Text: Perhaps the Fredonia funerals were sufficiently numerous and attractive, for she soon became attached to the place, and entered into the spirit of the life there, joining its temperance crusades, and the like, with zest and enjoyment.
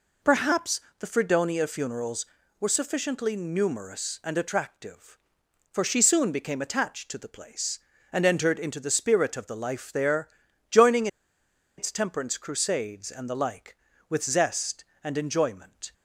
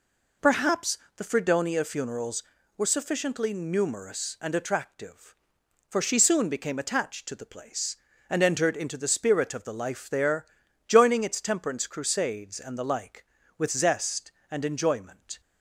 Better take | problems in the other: second | pauses between "Perhaps" and "the"; slight; at 0.7 s; 0.20 s long; slight in the second // pauses between "joining" and "its"; noticeable; at 11.0 s; 0.70 s long

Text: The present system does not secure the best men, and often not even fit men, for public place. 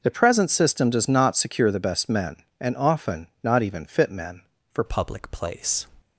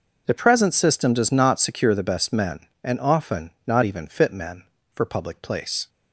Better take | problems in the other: second | pauses between "often" and "not"; slight; at 3.2 s; 0.16 s long; slight in the second // changes voice at "public"; from 4.8 s on; 1.0 s long

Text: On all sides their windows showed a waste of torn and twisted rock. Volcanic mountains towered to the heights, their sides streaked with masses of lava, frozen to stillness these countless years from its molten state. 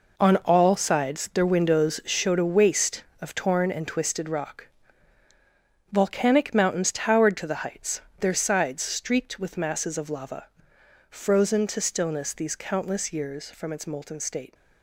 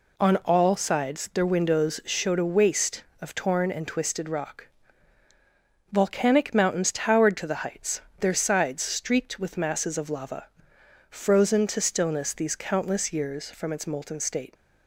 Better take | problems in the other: second | gets quieter; strong; throughout; 10.5 dB

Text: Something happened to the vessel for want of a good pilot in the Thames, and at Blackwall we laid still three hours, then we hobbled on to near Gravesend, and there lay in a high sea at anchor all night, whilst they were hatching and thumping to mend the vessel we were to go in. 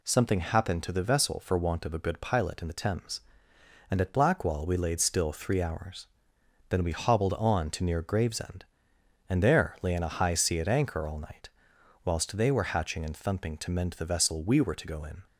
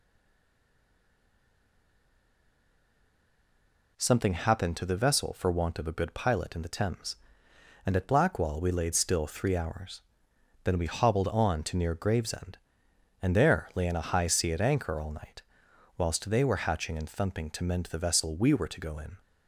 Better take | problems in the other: first | stays silent before the first word; strong; until 3.9 s; 3.9 s long

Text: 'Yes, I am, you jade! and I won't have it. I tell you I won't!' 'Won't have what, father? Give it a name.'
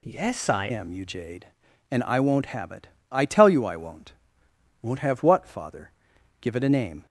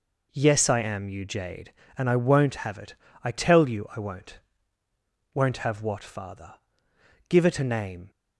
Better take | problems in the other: second | changes voice at "am"; from 0.6 s on; 6.4 s long

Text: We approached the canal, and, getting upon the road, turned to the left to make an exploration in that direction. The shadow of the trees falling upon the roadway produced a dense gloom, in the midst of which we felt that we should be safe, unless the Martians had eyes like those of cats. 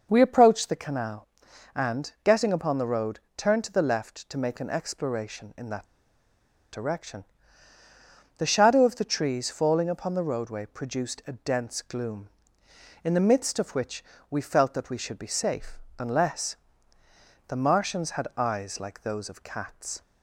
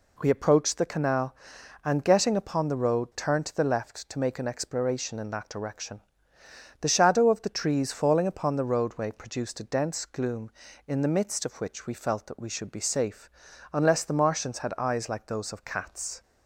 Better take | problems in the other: second | pauses between "that" and "direction"; noticeable; at 5.8 s; 0.86 s long // pauses between "which" and "we"; slight; at 14.0 s; 0.26 s long // pauses between "unless" and "the"; noticeable; at 16.5 s; 0.94 s long

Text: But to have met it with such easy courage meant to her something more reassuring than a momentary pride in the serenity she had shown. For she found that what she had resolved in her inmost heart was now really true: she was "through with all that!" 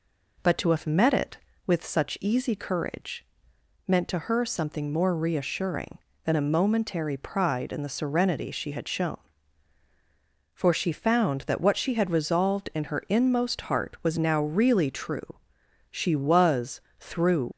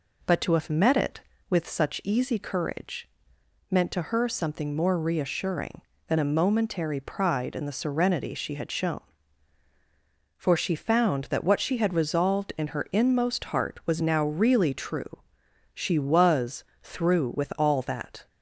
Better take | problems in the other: second | pauses between "courage" and "meant"; noticeable; at 3.2 s; 0.62 s long; noticeable in the second // pauses between "was" and "through"; slight; at 16.7 s; 0.20 s long; slight in the second // stops before "with all that"; at 17.5 s

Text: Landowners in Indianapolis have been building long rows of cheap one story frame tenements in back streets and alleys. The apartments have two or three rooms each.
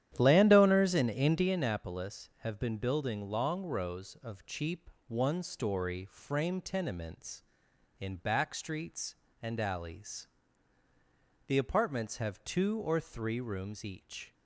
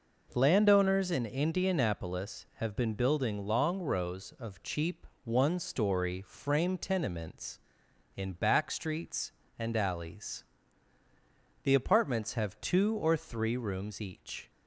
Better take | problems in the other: second | starts louder than the rest; strong; until 1.6 s; 11 dB // pauses between "cheap" and "one"; slight; at 4.9 s; 0.16 s long; slight in the second

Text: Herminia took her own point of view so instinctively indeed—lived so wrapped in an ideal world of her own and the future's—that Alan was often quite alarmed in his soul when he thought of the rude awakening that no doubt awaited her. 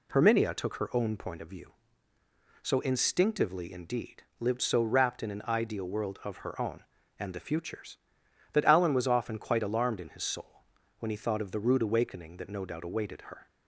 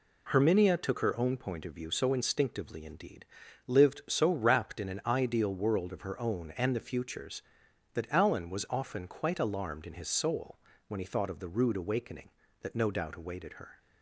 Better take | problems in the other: neither | pauses between "soul" and "when"; the same in both

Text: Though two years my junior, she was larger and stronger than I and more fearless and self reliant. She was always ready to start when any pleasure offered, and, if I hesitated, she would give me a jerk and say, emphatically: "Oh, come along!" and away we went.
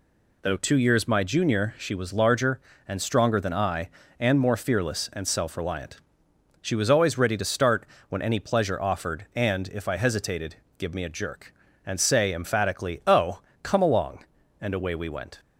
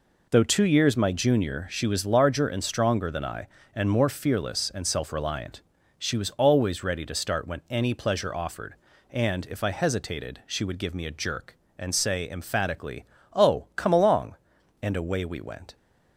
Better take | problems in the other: second | pauses between "start" and "when"; slight; at 7.8 s; 0.24 s long // skips "she would"; at 10.6 s

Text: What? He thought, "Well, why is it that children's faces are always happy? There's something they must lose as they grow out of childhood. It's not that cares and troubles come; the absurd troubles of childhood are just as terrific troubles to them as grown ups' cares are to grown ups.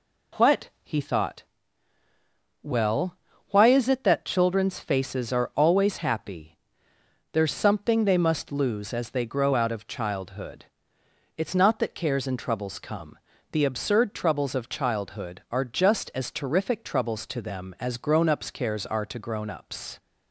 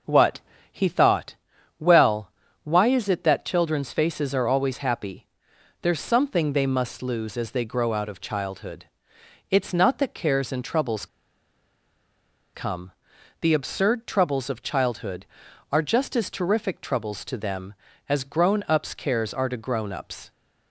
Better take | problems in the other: first | pauses between "troubles" and "come"; strong; at 11.0 s; 1.4 s long

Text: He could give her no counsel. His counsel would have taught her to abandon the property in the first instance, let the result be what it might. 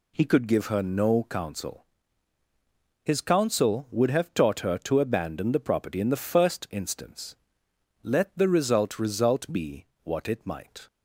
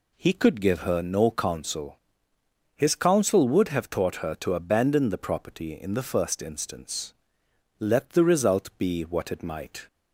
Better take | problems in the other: second | says "result" twice; at 8.9 s // pauses between "be" and "what"; slight; at 9.8 s; 0.18 s long

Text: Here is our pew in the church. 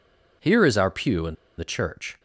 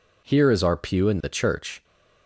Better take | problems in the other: second | pauses between "in" and "the"; slight; at 1.3 s; 0.22 s long

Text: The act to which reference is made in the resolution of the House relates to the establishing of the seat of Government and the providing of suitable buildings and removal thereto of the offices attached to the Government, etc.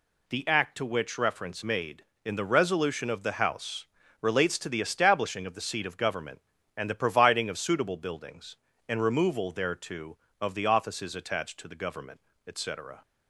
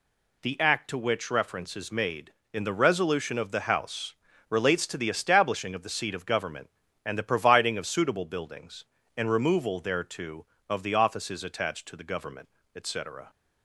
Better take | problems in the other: second | skips "is"; at 1.6 s // pauses between "House" and "relates"; slight; at 3.8 s; 0.36 s long; slight in the second

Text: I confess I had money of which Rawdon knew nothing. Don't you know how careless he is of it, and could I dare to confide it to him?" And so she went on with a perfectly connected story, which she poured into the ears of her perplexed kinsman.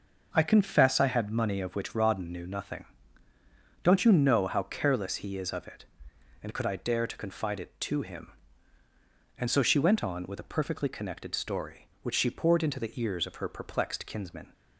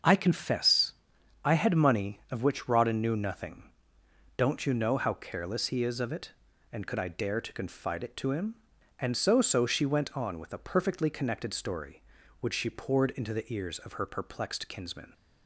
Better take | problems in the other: first | starts louder than the rest; until 1.5 s; 6.5 dB // pauses between "confess" and "I"; noticeable; at 0.9 s; 0.50 s long // says "so" twice; at 9.4 s

